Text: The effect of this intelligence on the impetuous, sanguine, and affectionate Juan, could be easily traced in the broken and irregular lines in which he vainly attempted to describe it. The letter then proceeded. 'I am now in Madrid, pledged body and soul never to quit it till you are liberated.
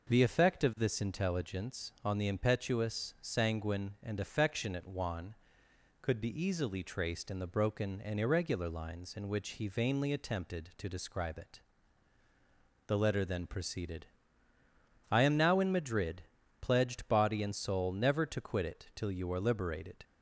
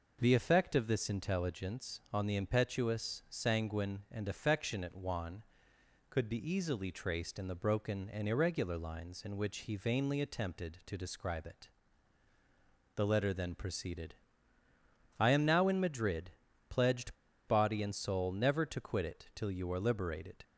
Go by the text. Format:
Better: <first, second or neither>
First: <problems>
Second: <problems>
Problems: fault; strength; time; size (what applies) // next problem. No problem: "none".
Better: first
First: none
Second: pauses between "pledged" and "body"; slight; at 17.1 s; 0.31 s long